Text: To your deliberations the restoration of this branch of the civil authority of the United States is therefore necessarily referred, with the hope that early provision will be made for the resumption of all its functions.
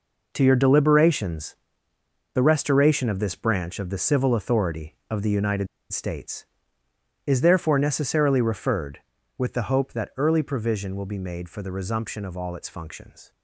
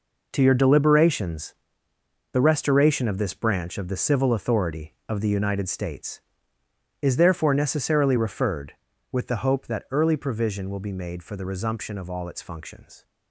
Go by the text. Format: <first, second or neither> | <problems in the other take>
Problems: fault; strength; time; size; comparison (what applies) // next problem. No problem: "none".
second | pauses between "deliberations" and "the"; noticeable; at 1.5 s; 0.76 s long; noticeable in the second // pauses between "United" and "States"; slight; at 5.6 s; 0.24 s long